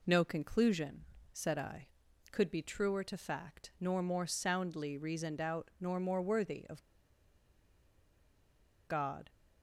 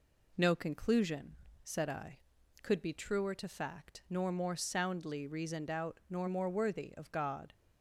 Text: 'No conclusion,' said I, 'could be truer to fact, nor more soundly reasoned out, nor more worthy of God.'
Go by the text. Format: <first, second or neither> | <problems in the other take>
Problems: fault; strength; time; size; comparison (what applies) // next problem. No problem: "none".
second | pauses between "of" and "God"; strong; at 6.8 s; 2.0 s long